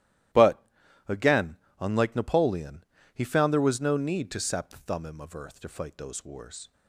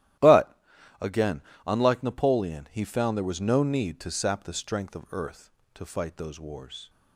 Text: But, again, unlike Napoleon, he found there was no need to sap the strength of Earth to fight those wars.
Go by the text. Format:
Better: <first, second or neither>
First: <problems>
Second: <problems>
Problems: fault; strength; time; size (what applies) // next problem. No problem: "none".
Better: second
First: starts louder than the rest; strong; until 2.0 s; 14.5 dB // says "thummim" for "strength"; at 4.7 s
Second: starts louder than the rest; strong; until 1.8 s; 13.5 dB